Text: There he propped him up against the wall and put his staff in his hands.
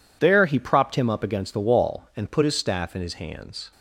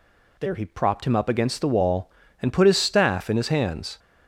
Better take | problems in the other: neither | none

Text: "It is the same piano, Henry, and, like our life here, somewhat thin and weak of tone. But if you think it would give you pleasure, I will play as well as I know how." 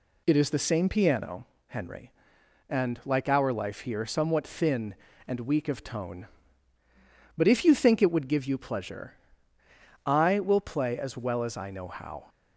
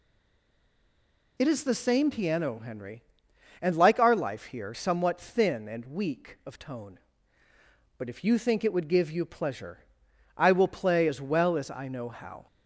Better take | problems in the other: first | stays silent before the first word; noticeable; until 1.3 s; 1.3 s long

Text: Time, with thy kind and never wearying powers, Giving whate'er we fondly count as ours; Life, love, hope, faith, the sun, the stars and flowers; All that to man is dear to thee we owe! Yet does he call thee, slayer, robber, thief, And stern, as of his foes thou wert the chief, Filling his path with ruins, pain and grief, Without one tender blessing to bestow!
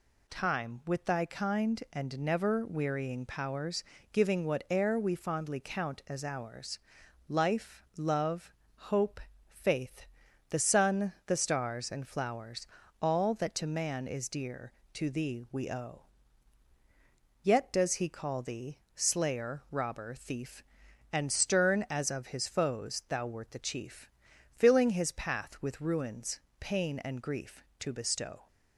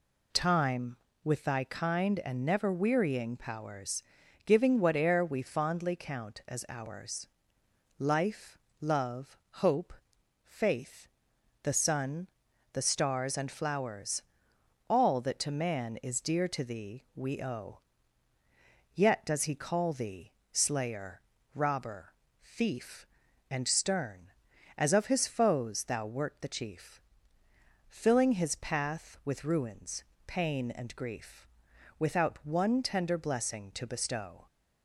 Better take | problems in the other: second | skips "Without one tender blessing"; at 27.7 s

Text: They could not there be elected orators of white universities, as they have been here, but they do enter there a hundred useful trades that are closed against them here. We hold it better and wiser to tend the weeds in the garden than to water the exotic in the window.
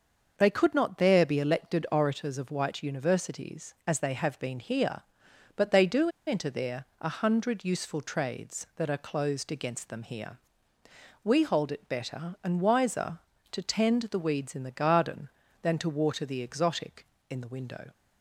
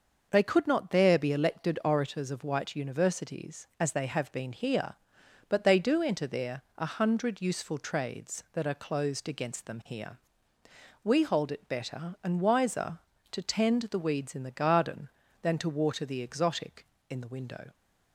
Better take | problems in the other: second | starts louder than the rest; noticeable; until 1.3 s; 6 dB; noticeable in the second // pauses between "do" and "enter"; slight; at 6.0 s; 0.18 s long // pauses between "there" and "a"; slight; at 6.8 s; 0.16 s long; slight in the second

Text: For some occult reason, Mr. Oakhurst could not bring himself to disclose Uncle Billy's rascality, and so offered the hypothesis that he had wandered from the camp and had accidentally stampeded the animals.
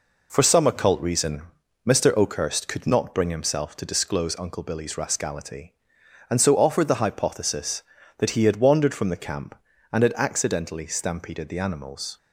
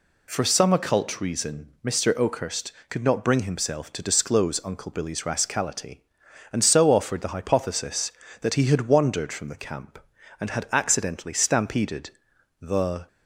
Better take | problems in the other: first | pauses between "stampeded" and "the"; noticeable; at 12.1 s; 0.50 s long // stops before "animals"; at 13.0 s

